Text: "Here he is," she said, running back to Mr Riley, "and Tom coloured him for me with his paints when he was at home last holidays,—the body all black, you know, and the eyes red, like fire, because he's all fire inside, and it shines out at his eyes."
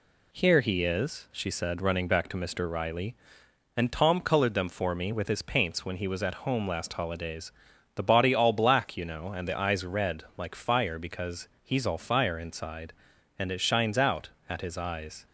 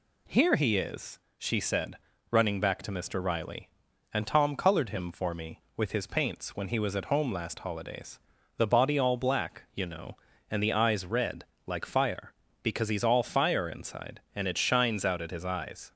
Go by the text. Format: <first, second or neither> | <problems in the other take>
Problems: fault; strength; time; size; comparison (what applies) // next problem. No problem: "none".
second | says "them" for "him"; at 4.5 s // pauses between "because" and "he's"; slight; at 11.4 s; 0.16 s long